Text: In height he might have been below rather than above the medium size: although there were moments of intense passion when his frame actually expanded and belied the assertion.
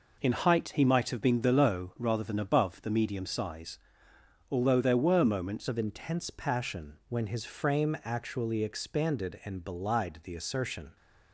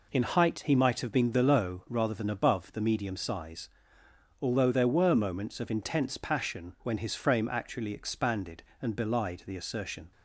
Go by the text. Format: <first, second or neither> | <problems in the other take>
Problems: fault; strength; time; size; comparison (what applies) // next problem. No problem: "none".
second | changes voice at "of"; from 5.6 s on; 5.3 s long